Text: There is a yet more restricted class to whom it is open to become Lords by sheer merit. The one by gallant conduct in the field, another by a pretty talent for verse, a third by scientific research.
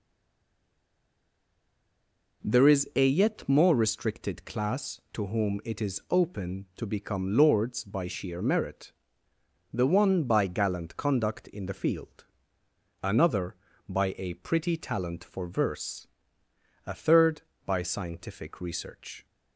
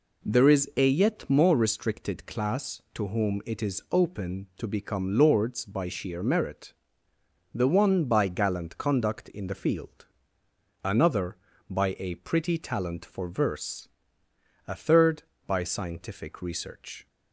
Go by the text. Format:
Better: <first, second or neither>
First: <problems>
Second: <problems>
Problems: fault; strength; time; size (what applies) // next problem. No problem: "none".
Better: second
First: stays silent before the first word; until 2.4 s; 2.4 s long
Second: none